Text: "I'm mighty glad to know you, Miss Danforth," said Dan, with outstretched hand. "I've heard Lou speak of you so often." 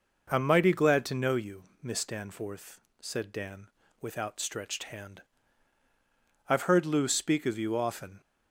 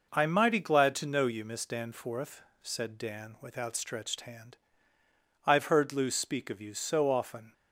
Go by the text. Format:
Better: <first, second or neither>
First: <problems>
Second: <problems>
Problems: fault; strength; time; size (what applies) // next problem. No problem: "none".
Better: second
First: skips "so"; at 7.7 s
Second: none